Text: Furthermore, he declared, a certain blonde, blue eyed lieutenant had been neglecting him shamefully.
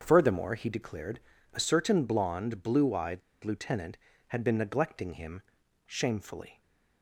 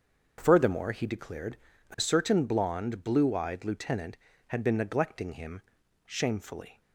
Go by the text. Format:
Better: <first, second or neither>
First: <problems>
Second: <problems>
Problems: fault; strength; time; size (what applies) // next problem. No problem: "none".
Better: second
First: starts louder than the rest; until 1.0 s; 7 dB // pauses between "eyed" and "lieutenant"; slight; at 3.2 s; 0.22 s long // pauses between "him" and "shamefully"; at 5.4 s; 0.44 s long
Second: starts louder than the rest; until 1.3 s; 7 dB // pauses between "him" and "shamefully"; at 5.6 s; 0.44 s long